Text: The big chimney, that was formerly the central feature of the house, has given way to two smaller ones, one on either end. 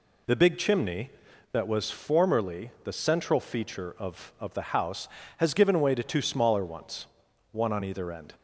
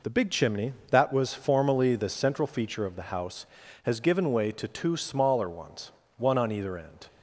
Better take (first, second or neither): second